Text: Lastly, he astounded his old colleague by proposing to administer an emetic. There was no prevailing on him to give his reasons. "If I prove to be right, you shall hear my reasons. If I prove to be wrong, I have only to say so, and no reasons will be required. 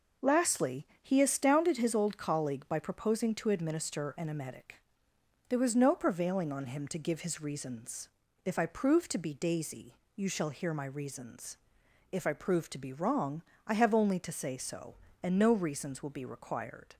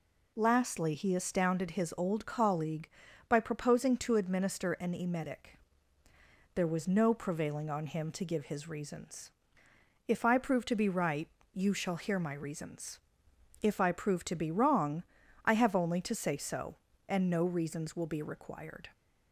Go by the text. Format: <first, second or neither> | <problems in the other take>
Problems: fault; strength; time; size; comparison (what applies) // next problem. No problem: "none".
second | says "daisy" for "right"; at 9.3 s